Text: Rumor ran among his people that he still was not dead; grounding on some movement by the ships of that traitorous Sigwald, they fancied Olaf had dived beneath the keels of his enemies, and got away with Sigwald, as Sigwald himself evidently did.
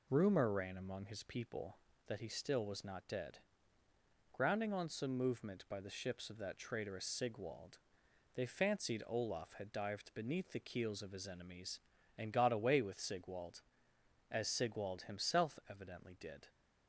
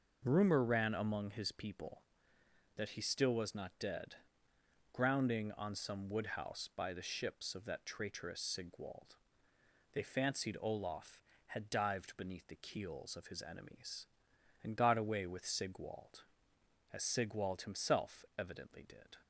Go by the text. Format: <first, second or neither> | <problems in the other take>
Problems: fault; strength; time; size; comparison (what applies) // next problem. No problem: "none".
first | says "woodhouse" for "movement"; at 6.0 s